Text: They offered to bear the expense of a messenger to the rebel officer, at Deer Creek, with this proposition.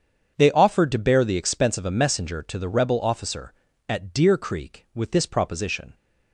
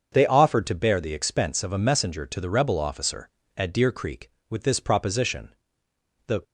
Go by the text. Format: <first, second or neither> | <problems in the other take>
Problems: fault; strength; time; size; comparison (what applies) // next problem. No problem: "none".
first | starts louder than the rest; until 1.1 s; 7 dB; strong in the first // goes on to say "The"; slight; from 6.2 s on; 0.16 s long